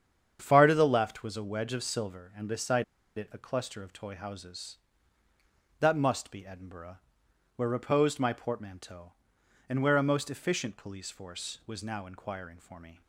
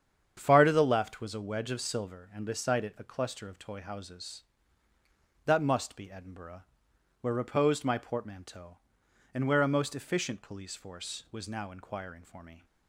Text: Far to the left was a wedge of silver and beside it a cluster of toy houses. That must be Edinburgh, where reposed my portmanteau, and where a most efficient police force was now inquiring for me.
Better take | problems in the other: second | starts louder than the rest; strong; until 1.4 s; 8 dB; strong in the second // pauses between "beside" and "it"; slight; at 2.8 s; 0.33 s long

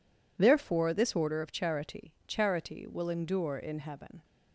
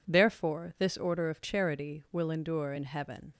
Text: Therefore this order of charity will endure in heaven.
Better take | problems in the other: second | says "charity" twice; at 2.2 s

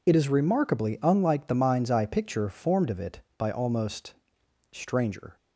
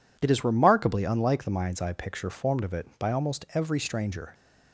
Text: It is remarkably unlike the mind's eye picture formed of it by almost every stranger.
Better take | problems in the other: second | skips "every"; at 4.4 s

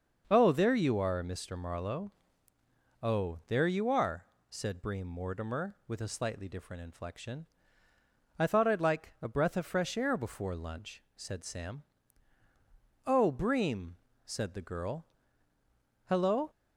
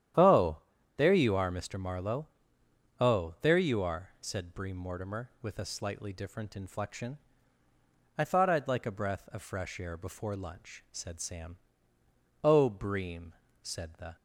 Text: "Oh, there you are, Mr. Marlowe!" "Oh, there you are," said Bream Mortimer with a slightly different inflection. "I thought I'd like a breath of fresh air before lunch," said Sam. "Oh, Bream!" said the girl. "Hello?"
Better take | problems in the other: first | starts louder than the rest; strong; until 1.5 s; 10 dB; also in the first // stops before "girl Hello"; at 14.1 s

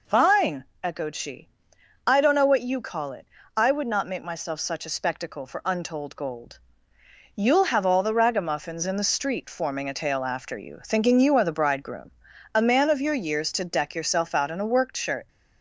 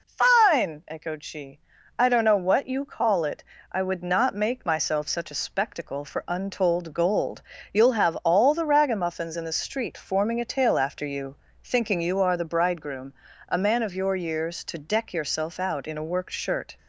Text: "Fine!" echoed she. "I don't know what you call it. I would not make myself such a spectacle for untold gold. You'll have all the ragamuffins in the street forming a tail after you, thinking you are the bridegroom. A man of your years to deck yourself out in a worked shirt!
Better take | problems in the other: neither | none

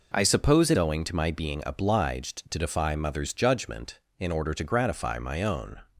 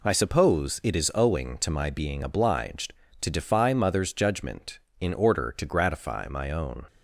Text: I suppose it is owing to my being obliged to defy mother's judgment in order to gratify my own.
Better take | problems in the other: second | skips "is"; at 0.7 s

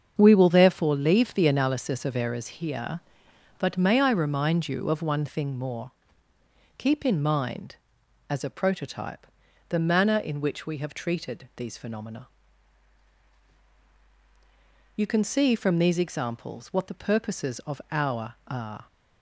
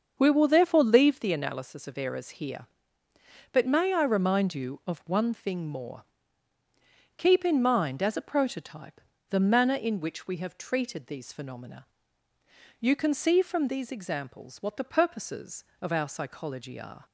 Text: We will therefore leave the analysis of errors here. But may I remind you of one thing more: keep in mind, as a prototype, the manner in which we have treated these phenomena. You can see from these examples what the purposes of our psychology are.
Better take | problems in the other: second | starts louder than the rest; until 1.1 s; 7 dB; also in the second // skips "psychology"; at 18.4 s

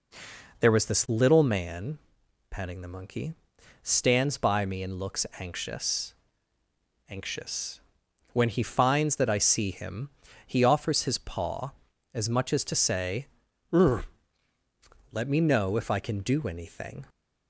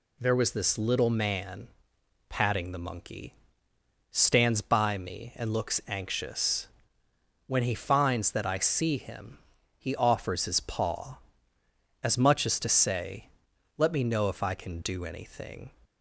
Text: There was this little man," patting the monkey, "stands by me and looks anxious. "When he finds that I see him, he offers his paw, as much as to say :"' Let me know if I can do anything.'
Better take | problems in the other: second | says "anxious" twice; at 7.0 s

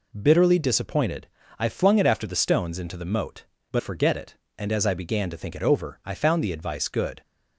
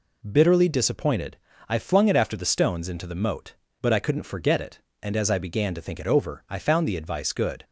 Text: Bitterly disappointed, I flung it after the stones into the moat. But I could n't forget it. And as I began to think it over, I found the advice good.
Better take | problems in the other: second | skips "I could n't"; at 3.8 s

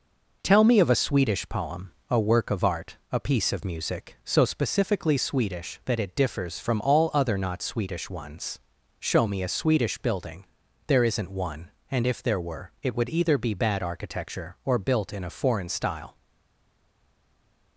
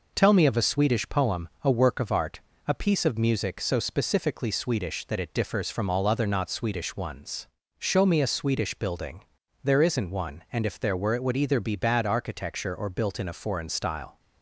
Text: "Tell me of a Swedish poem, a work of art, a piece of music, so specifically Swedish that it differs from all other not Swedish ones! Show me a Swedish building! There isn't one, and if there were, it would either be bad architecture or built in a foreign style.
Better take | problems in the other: second | stays silent after the last word; noticeable; from 16.1 s on; 1.6 s long

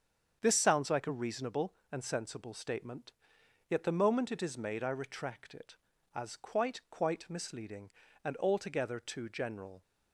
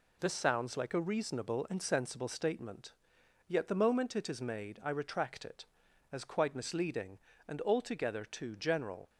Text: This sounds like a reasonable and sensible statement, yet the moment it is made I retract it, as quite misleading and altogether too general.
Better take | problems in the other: second | starts louder than the rest; strong; until 1.4 s; 7.5 dB // says "quite" twice; at 6.9 s

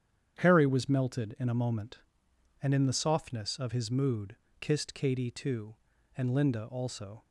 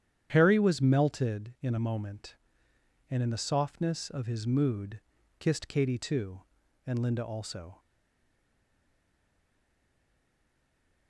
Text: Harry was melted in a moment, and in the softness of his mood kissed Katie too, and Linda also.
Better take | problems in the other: first | starts louder than the rest; strong; until 1.3 s; 9.5 dB; strong in the first // pauses between "mood" and "kissed"; at 4.9 s; 0.40 s long; slight in the first // stays silent after the last word; strong; from 7.7 s on; 3.3 s long

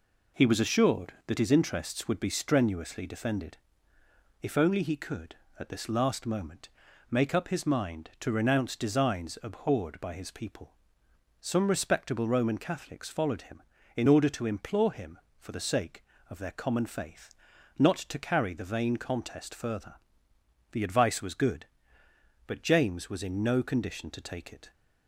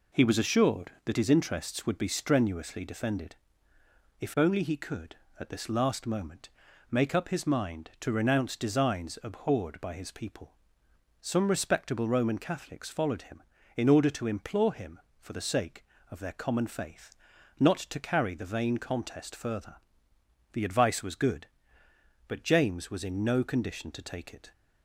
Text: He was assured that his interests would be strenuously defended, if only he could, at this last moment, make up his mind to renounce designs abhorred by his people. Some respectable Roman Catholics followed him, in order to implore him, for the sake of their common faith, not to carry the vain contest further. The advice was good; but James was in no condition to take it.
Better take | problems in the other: neither | none

